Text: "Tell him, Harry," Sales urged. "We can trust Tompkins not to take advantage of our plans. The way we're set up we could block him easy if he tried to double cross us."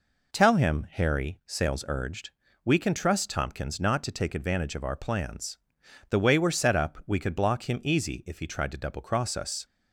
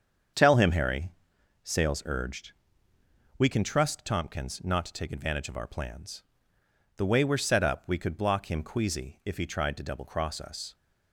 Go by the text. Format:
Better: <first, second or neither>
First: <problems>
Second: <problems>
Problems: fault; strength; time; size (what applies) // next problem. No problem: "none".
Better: first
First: none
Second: starts louder than the rest; strong; until 1.8 s; 7.5 dB // says "queasy" for "easy"; at 8.6 s